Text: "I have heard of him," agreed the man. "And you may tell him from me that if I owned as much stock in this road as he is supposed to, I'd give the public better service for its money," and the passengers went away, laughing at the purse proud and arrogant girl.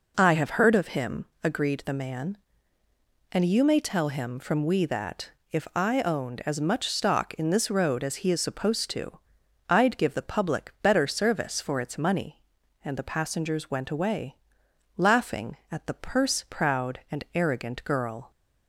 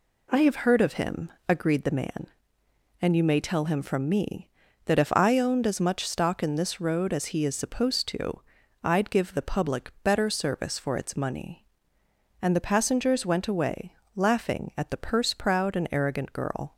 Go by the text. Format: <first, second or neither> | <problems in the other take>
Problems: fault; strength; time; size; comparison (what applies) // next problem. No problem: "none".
second | says "we" for "me"; at 4.6 s // pauses between "that" and "if"; slight; at 5.3 s; 0.20 s long